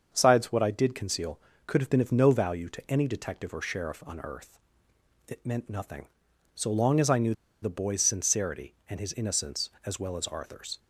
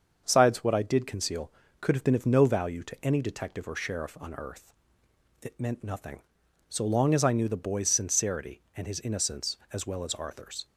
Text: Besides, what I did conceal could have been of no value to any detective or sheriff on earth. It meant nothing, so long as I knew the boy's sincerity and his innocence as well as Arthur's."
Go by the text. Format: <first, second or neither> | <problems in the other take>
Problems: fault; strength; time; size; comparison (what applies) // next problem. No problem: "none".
second | starts louder than the rest; until 1.1 s; 6.5 dB; also in the second // pauses between "knew" and "the"; slight; at 7.3 s; 0.29 s long